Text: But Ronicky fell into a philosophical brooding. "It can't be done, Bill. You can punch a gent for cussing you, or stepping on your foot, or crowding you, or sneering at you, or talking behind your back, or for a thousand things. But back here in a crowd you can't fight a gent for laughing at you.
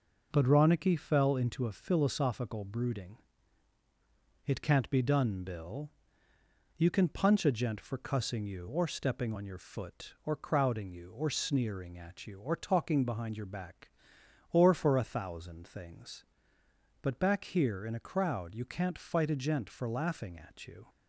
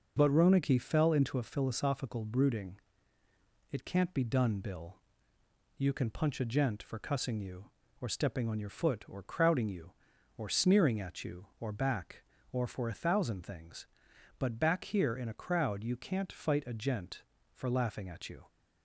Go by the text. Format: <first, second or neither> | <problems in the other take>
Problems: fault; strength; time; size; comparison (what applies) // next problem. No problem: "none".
first | skips "talking behind your"; at 11.7 s